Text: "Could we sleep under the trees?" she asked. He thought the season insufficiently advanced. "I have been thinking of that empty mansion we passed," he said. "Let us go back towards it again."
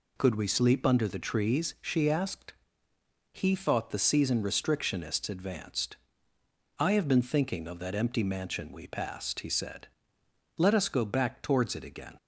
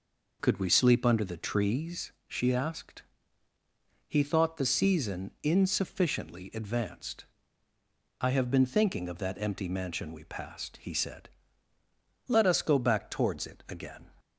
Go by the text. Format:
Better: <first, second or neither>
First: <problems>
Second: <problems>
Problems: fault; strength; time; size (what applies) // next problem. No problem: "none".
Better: second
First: says "restrictionists" for "insufficiently"; at 4.4 s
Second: none